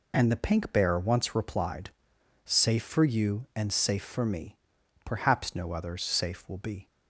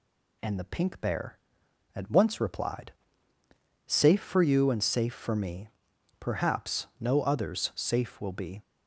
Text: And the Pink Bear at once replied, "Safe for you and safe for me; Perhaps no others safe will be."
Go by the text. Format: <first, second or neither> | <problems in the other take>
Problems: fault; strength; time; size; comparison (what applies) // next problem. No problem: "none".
second | skips "at"; at 0.9 s